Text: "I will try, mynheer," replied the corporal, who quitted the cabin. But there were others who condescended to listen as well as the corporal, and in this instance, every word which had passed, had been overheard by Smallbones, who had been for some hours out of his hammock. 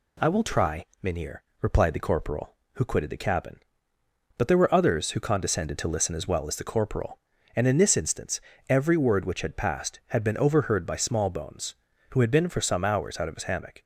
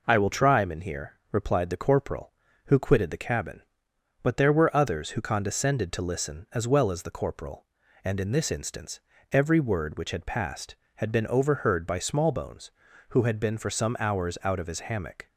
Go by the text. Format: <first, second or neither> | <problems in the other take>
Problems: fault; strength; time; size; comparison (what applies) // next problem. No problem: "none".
neither | none